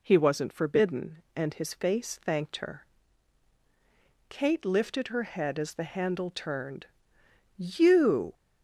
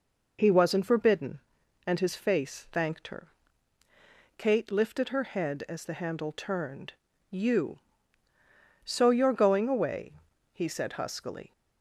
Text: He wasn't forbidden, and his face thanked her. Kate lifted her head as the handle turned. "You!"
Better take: first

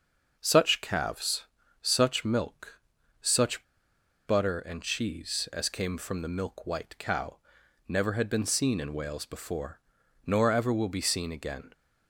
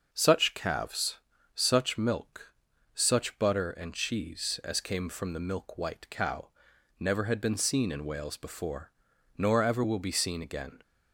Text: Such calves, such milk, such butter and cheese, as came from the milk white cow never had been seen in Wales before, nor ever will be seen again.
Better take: second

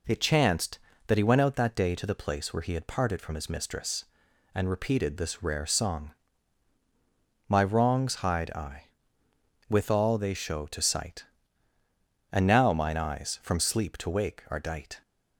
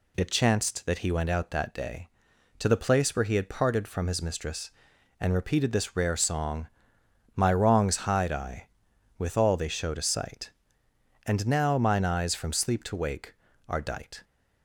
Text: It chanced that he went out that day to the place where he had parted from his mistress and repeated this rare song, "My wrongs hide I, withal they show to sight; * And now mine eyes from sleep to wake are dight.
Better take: neither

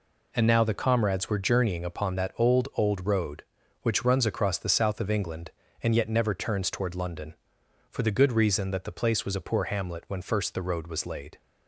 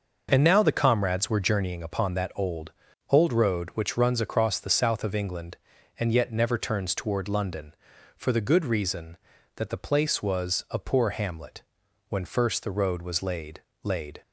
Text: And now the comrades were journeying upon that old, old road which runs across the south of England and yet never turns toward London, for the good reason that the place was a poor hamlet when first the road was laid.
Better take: first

